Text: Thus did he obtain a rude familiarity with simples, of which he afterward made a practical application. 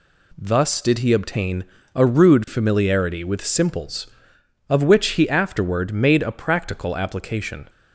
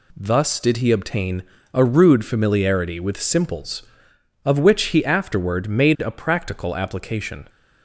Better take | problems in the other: neither | pauses between "obtain" and "a"; slight; the same in both

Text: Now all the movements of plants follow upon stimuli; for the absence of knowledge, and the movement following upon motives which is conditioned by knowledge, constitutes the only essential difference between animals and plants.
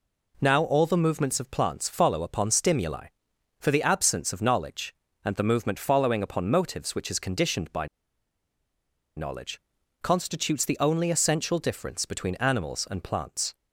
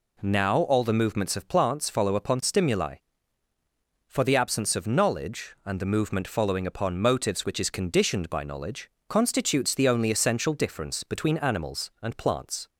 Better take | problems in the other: second | pauses between "by" and "knowledge"; strong; at 7.8 s; 1.3 s long

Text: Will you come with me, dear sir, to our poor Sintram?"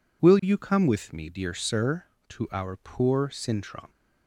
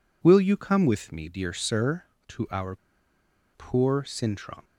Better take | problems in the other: first | pauses between "our" and "poor"; noticeable; at 2.7 s; 0.77 s long

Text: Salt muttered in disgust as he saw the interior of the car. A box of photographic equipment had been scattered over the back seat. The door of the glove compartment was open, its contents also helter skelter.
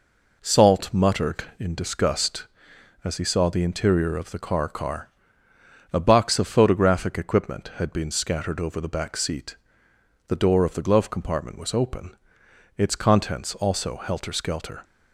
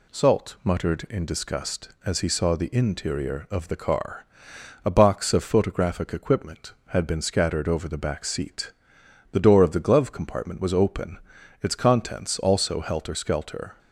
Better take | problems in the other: second | says "car" twice; at 4.6 s

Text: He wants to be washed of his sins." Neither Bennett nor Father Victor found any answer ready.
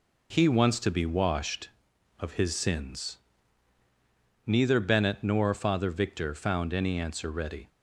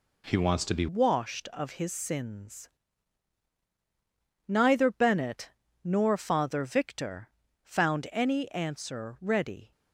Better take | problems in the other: first | changes voice at "washed"; from 0.8 s on; 8.9 s long // pauses between "Bennett" and "nor"; slight; at 5.5 s; 0.30 s long // pauses between "Victor" and "found"; slight; at 7.2 s; 0.34 s long

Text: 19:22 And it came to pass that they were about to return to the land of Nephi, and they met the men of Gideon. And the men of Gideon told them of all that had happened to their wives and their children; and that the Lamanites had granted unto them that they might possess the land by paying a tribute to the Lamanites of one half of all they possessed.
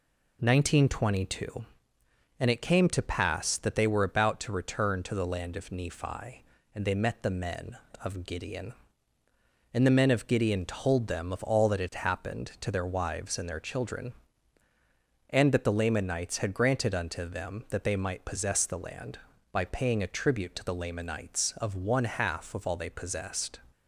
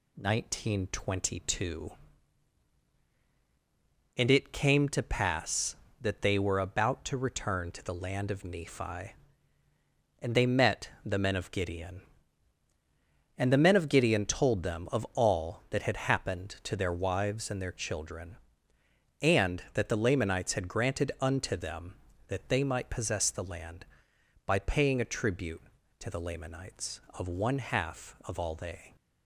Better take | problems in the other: first | stops before "possessed"; at 28.9 s

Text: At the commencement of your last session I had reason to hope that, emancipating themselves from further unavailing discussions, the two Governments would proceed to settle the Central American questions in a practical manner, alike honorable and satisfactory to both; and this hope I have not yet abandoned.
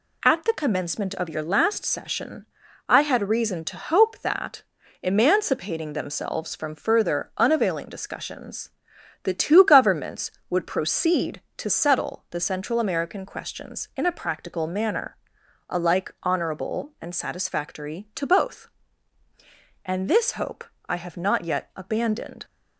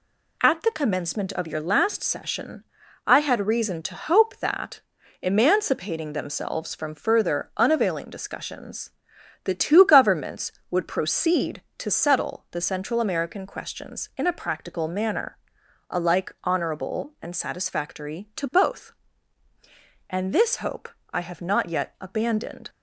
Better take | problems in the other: neither | pauses between "session" and "I"; the same in both // pauses between "hope" and "I"; slight; the same in both

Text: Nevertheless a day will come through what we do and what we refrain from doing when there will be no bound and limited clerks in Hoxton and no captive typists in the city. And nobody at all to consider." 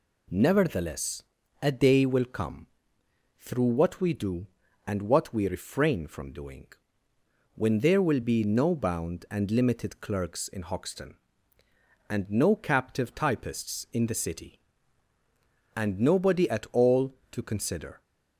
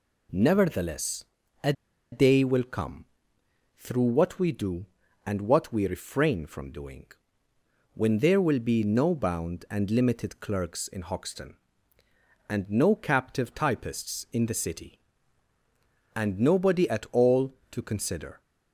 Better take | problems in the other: first | pauses between "Nevertheless" and "a"; at 1.2 s; 0.40 s long; also in the first // pauses between "a" and "day"; at 1.7 s; 0.40 s long // pauses between "come" and "through"; noticeable; at 3.0 s; 0.74 s long; noticeable in the first // pauses between "doing" and "when"; noticeable; at 7.0 s; 0.88 s long; noticeable in the first

